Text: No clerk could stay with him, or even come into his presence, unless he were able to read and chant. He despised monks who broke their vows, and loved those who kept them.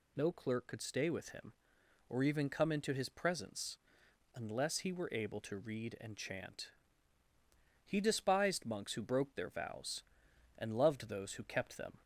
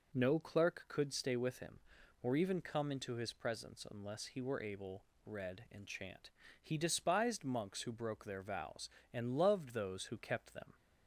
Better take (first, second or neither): first